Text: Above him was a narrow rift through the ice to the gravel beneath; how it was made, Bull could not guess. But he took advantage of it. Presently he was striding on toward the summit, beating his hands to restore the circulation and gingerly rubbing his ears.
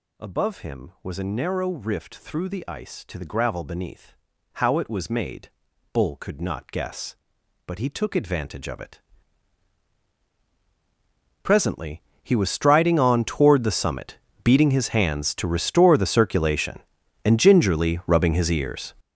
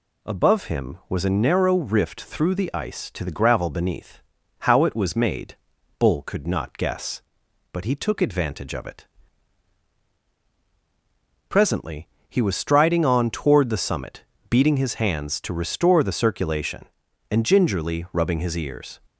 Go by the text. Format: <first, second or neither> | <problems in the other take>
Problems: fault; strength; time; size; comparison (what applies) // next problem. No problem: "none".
second | gets louder; strong; throughout; 12.5 dB // pauses between "Presently" and "he"; slight; at 11.9 s; 0.22 s long; slight in the second